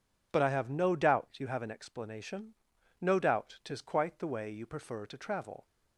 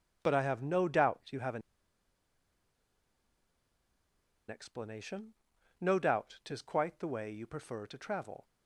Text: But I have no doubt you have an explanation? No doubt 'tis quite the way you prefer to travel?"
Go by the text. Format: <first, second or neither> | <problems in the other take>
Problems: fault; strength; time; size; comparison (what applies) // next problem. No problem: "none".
first | pauses between "an" and "explanation"; strong; at 1.6 s; 2.8 s long